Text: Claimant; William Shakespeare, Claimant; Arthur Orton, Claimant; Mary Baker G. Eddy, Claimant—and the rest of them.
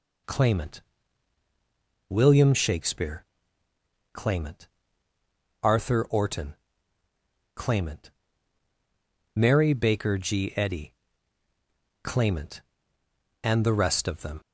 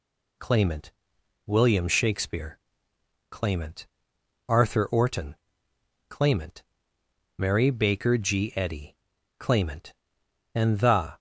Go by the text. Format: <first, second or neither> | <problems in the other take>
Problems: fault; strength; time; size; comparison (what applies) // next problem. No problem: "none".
first | stops before "rest of them"; at 11.1 s